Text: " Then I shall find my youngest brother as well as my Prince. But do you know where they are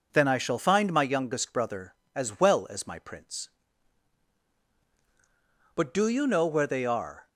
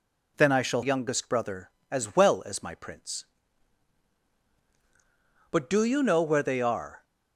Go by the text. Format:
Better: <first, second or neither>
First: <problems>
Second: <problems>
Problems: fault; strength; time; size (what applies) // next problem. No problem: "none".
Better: first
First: none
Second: skips "find my"; at 0.8 s